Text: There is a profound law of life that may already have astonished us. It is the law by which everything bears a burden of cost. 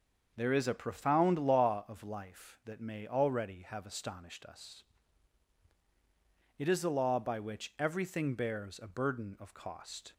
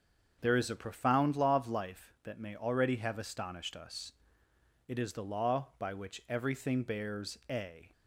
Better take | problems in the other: first | starts louder than the rest; until 1.4 s; 6.5 dB; also in the first // stops before "burden of cost"; at 7.9 s

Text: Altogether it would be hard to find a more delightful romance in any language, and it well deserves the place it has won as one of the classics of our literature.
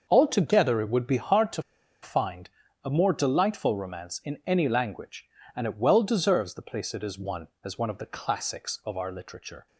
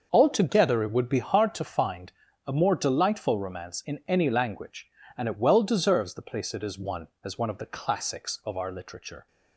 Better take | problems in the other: second | starts louder than the rest; noticeable; until 1.0 s; 6 dB; noticeable in the second // pauses between "to" and "find"; at 1.6 s; 0.41 s long // pauses between "find" and "a"; slight; at 2.4 s; 0.36 s long; slight in the second

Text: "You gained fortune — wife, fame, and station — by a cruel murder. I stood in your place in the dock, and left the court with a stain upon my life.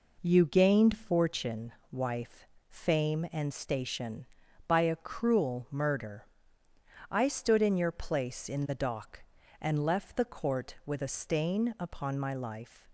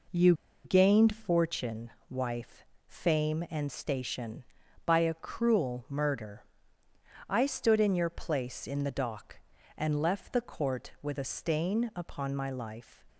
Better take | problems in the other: first | pauses between "You" and "gained"; slight; at 0.3 s; 0.31 s long

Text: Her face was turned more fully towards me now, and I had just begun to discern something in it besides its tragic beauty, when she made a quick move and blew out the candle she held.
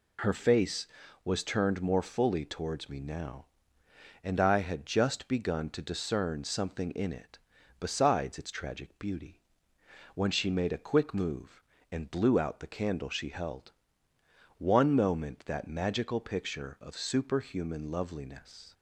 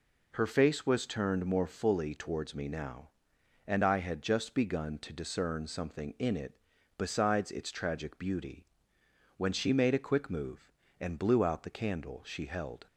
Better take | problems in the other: second | pauses between "it" and "besides"; at 7.3 s; 0.42 s long; also in the second // goes on to say "One moment that magical picture of superhuman loveliness"; strong; from 14.5 s on; 4.1 s long

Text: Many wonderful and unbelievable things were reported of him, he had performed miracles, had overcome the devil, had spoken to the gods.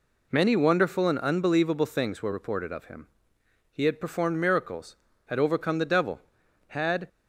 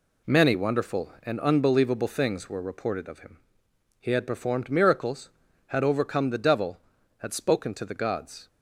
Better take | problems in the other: second | stops before "spoken to the gods"; at 7.0 s

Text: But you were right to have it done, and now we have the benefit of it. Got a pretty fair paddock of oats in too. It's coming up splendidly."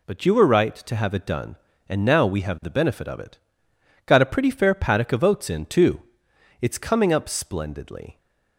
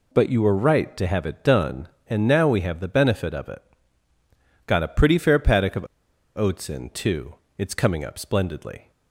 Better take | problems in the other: first | pauses between "of" and "oats"; noticeable; at 5.8 s; 0.51 s long

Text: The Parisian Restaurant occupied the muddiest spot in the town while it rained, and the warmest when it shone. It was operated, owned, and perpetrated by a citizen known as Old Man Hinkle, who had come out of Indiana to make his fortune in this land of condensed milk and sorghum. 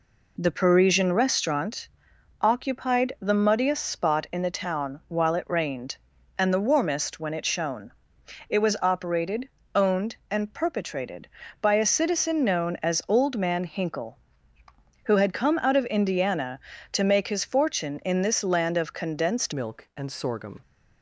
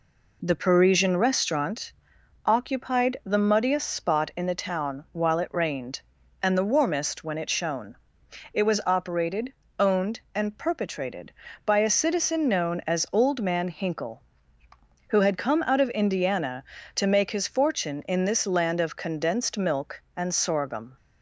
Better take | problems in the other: second | pauses between "Restaurant" and "occupied"; noticeable; at 1.8 s; 0.54 s long; noticeable in the second // changes voice at "milk"; from 19.5 s on; 1.1 s long

